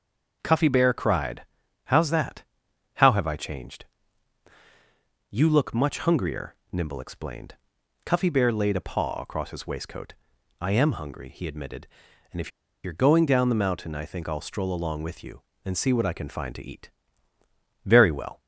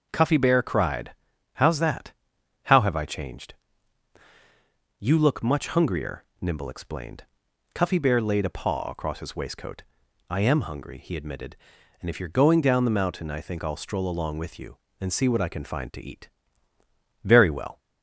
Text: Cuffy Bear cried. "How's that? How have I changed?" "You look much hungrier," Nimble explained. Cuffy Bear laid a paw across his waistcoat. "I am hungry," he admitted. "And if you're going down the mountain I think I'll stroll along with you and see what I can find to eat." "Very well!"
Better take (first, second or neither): second